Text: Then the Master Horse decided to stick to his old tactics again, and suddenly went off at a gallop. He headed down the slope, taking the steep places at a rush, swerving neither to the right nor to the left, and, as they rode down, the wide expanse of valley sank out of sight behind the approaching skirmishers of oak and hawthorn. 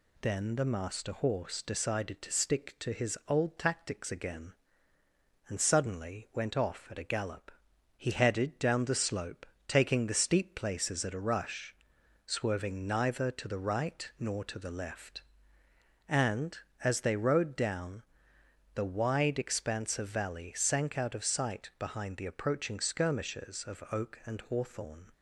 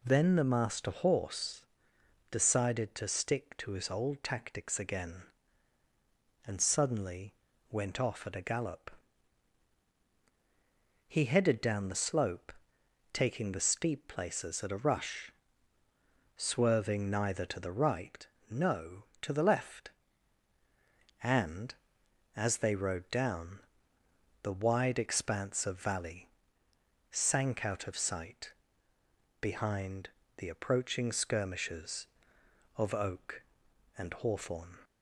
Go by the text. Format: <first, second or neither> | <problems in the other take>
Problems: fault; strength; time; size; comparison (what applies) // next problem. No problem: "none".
first | pauses between "Horse" and "decided"; noticeable; at 1.6 s; 0.68 s long // pauses between "suddenly" and "went"; at 7.3 s; 0.36 s long // says "no" for "nor"; at 18.4 s // pauses between "valley" and "sank"; noticeable; at 26.2 s; 0.82 s long // pauses between "sight" and "behind"; noticeable; at 28.5 s; 0.90 s long // pauses between "behind" and "the"; slight; at 30.0 s; 0.28 s long